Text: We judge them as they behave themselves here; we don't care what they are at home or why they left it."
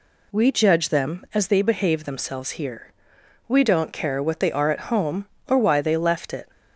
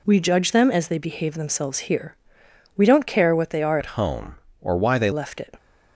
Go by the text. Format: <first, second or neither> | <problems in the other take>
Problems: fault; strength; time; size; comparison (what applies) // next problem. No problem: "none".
first | changes voice from "at" to "they"; from 3.7 to 5.1 s; 1.4 s long